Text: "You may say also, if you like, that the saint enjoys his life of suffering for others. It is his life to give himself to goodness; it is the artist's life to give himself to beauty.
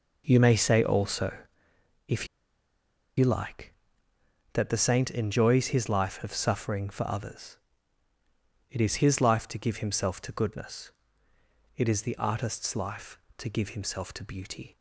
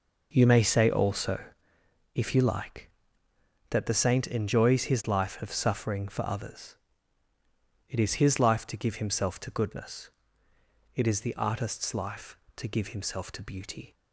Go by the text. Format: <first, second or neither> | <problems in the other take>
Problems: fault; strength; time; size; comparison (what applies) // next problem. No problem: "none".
second | pauses between "if" and "you"; noticeable; at 2.2 s; 0.90 s long